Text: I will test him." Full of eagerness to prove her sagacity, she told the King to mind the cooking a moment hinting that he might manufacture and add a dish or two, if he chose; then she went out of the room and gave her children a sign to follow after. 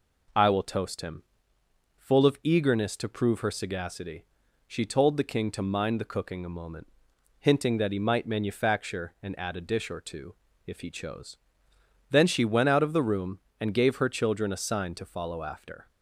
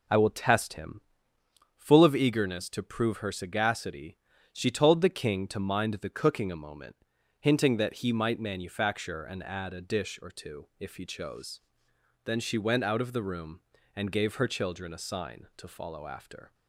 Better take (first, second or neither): second